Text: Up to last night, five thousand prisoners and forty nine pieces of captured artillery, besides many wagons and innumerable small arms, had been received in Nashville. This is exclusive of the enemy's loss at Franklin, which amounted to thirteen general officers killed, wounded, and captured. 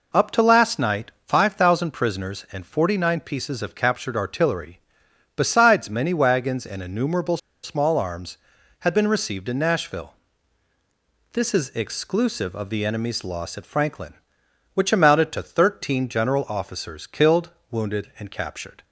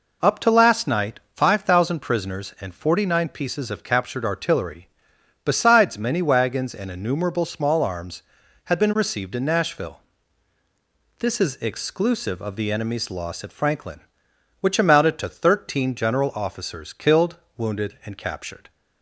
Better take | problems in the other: second | pauses between "innumerable" and "small"; slight; at 7.3 s; 0.25 s long

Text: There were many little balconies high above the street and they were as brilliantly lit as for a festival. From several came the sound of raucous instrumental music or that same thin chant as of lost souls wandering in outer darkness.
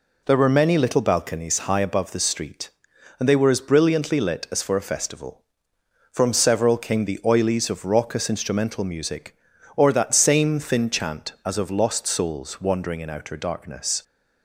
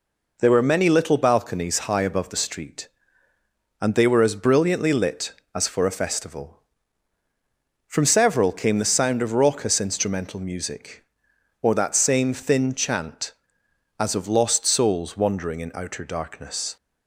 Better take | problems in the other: second | says "oilies" for "sound"; at 7.2 s

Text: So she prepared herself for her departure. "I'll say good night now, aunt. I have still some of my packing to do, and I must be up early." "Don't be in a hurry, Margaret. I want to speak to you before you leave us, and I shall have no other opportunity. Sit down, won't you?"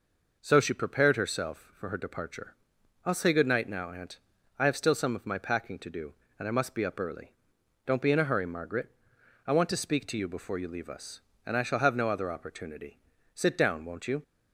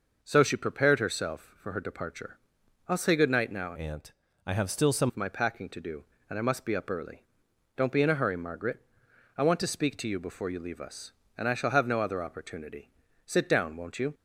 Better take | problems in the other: first | changes voice from "aunt" to "some"; from 3.7 to 5.0 s; 1.3 s long

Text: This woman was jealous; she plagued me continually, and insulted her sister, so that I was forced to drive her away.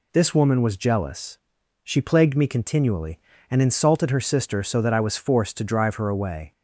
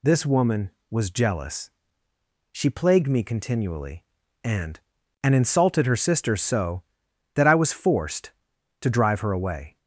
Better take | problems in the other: first | says "and" twice; at 5.2 s

